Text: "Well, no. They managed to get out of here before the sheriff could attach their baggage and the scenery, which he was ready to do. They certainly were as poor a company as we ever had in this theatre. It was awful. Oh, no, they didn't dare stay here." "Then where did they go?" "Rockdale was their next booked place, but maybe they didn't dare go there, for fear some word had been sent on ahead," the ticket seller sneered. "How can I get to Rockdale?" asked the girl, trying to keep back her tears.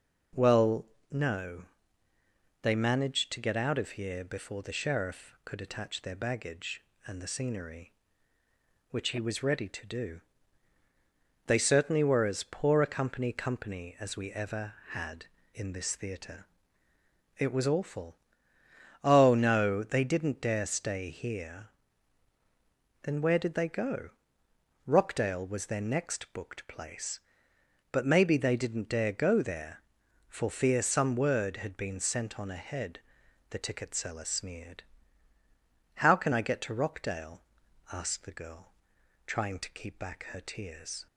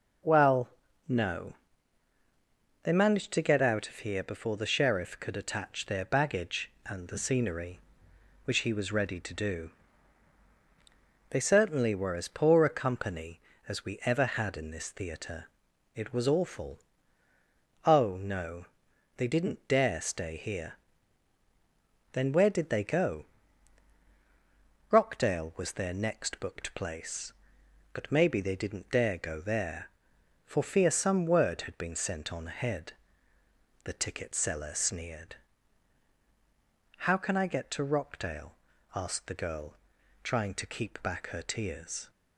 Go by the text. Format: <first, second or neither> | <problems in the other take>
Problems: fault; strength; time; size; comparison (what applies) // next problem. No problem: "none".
second | says "company" twice; at 13.3 s